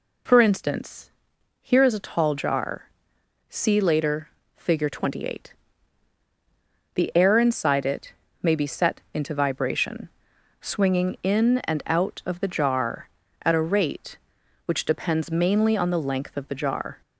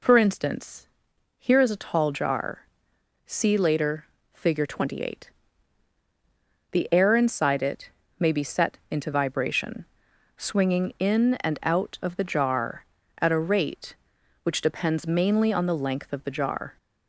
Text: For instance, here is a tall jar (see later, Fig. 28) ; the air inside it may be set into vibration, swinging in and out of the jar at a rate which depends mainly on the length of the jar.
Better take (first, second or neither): neither